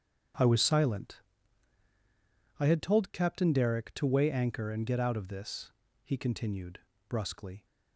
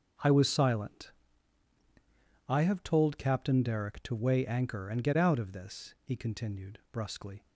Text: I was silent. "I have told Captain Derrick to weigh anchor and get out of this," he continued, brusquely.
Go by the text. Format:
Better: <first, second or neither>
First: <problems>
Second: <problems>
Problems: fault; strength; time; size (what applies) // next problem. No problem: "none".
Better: second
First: starts louder than the rest; strong; until 2.7 s; 8 dB // says "had" for "have"; at 2.6 s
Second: starts louder than the rest; until 2.5 s; 7 dB